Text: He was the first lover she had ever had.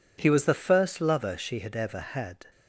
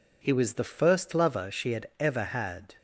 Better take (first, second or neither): neither